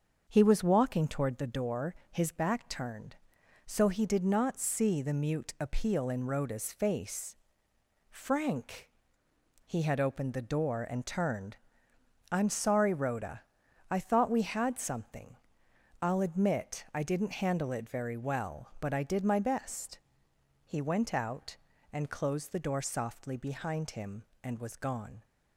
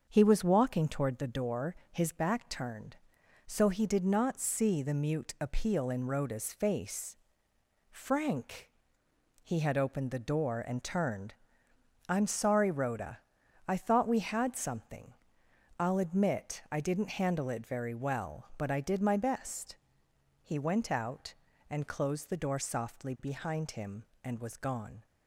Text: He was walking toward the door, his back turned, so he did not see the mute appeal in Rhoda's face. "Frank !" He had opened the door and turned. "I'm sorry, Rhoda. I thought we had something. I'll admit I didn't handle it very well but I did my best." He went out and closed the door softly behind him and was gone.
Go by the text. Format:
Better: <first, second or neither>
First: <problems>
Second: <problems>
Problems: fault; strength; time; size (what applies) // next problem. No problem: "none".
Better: neither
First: starts louder than the rest; until 1.2 s; 6.5 dB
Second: starts louder than the rest; until 1.1 s; 6.5 dB